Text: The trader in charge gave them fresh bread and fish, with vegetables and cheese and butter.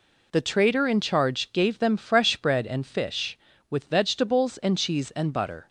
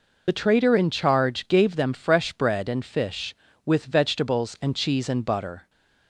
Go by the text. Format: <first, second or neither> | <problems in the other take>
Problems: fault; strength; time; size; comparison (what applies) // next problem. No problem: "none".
first | loses the start of "The"; at 0.2 s; 40 ms